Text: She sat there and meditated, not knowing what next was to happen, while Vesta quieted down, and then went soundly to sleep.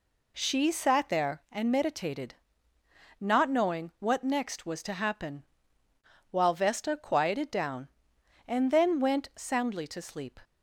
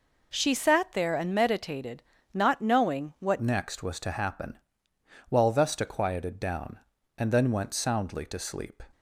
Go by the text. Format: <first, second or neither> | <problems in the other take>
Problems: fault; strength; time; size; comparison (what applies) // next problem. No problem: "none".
first | changes voice at "next"; from 3.4 s on; 5.4 s long